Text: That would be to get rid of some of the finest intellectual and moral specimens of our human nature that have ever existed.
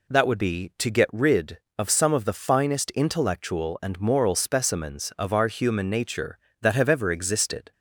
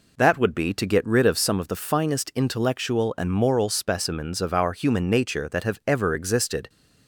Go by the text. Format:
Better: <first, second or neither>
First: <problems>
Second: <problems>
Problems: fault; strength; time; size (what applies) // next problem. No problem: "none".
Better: neither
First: none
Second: none